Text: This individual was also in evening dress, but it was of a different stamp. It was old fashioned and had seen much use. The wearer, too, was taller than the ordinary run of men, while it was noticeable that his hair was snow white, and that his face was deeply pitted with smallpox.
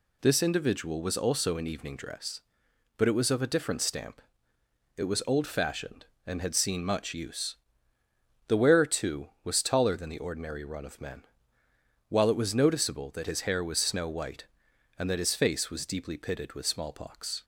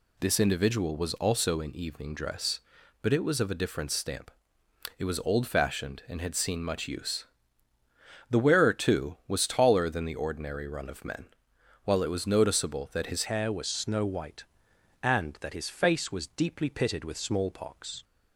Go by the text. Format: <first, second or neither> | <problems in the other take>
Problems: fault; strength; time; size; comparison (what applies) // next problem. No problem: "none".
first | changes voice at "hair"; from 13.2 s on; 4.8 s long